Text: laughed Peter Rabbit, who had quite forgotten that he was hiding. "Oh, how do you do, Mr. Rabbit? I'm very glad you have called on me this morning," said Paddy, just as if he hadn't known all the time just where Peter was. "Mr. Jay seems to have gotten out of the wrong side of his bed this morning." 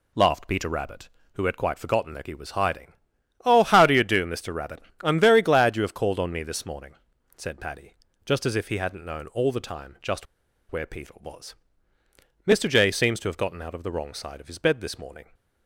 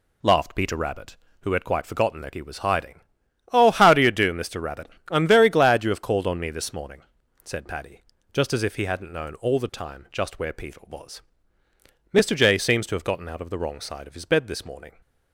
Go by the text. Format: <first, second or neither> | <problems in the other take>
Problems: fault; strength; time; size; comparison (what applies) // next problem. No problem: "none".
second | pauses between "just" and "where"; at 10.2 s; 0.45 s long